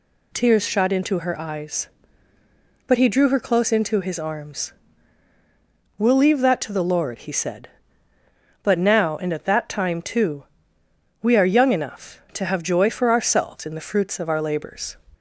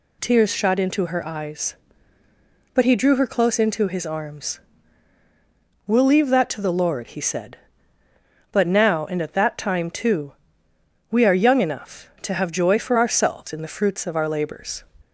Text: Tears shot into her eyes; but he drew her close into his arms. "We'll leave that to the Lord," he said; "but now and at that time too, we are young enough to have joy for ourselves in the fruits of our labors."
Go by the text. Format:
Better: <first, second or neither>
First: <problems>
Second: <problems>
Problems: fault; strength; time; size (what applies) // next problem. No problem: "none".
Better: neither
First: none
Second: none